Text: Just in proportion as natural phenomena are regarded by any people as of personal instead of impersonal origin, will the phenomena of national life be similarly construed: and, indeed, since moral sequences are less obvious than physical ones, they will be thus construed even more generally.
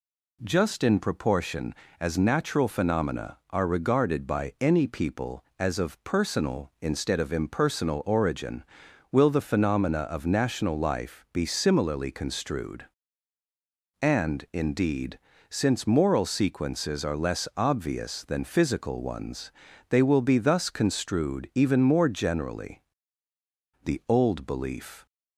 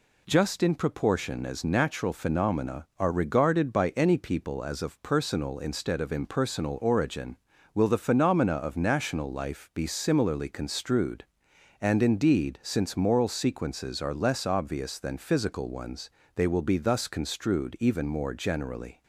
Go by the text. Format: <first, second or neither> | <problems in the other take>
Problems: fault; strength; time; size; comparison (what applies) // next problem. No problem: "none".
second | goes on to say "The old belief"; noticeable; from 23.8 s on; 1.2 s long